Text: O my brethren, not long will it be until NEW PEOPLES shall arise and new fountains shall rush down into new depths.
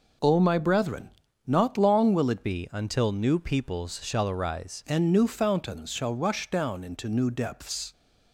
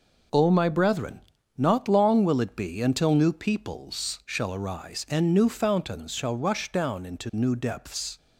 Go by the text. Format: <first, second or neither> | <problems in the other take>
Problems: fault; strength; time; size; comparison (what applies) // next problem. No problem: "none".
second | changes voice from "be" to "arise"; from 2.4 to 4.8 s; 2.4 s long